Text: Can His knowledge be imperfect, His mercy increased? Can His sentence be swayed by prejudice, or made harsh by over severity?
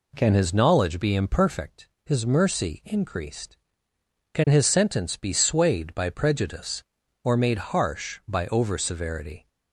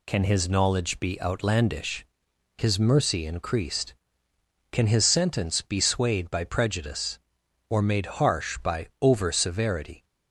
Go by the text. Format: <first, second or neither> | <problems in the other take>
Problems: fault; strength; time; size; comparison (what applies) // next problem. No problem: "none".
first | says "outlandish" for "imperfect"; at 1.2 s